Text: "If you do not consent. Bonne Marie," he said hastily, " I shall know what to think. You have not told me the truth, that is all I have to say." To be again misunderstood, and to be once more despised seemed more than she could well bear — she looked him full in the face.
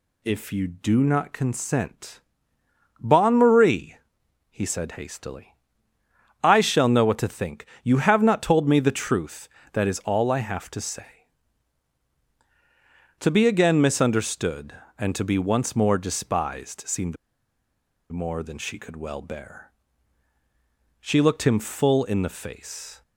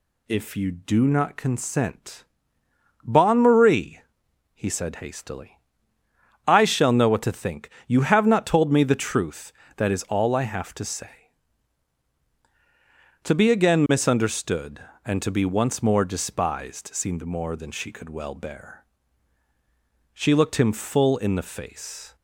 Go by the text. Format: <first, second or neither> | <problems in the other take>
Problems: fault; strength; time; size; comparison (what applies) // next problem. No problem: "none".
second | pauses between "seemed" and "more"; noticeable; at 17.1 s; 0.95 s long